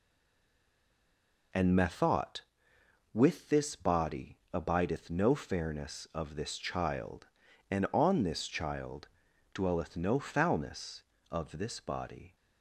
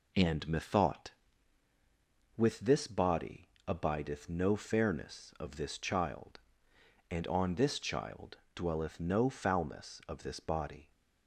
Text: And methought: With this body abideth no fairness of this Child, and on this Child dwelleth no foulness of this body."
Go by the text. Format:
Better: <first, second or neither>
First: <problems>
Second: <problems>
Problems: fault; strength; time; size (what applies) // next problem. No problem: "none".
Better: second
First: stays silent before the first word; noticeable; until 1.5 s; 1.5 s long // pauses between "body" and "abideth"; slight; at 4.3 s; 0.16 s long // pauses between "Child" and "dwelleth"; at 9.0 s; 0.42 s long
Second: pauses between "body" and "abideth"; slight; at 3.4 s; 0.18 s long // pauses between "Child" and "dwelleth"; slight; at 8.3 s; 0.16 s long